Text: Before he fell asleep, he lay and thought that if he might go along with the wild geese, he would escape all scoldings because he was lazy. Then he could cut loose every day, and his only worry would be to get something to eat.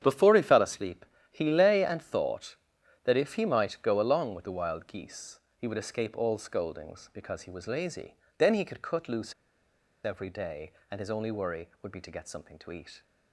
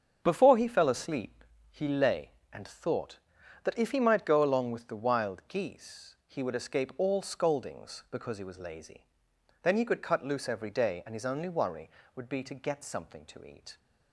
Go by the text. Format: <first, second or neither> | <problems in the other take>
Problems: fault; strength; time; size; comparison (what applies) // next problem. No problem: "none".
second | starts louder than the rest; strong; until 1.0 s; 9 dB; strong in the second // pauses between "loose" and "every"; noticeable; at 9.3 s; 0.71 s long